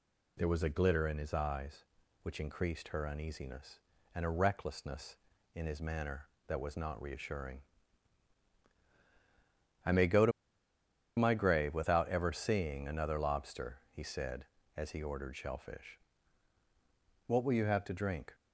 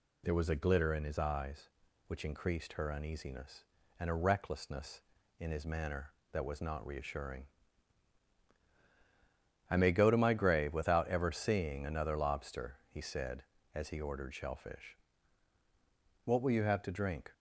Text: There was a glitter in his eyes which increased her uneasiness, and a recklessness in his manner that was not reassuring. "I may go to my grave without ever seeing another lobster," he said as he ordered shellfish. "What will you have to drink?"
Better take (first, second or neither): second